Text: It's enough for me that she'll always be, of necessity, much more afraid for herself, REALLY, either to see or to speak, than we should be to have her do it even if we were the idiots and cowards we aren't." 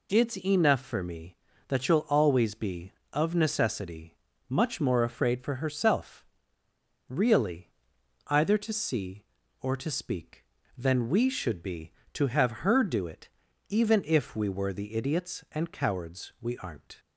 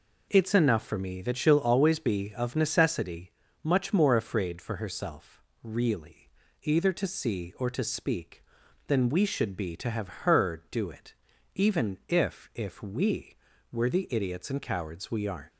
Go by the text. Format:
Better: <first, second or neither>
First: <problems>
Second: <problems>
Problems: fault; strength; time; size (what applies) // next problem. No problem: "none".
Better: first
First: pauses between "it" and "even"; at 13.2 s; 0.38 s long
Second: pauses between "it" and "even"; at 11.1 s; 0.40 s long // says "if" twice; at 12.5 s